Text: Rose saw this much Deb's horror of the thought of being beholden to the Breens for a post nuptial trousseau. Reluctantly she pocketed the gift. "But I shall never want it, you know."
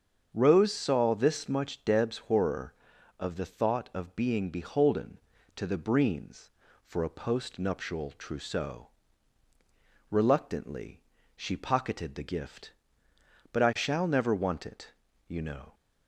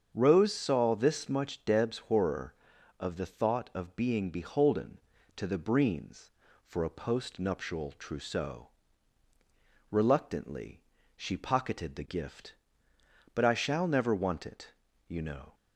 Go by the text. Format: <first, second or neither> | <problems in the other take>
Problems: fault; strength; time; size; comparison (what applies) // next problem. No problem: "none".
neither | starts louder than the rest; strong; the same in both // pauses between "Reluctantly" and "she"; slight; the same in both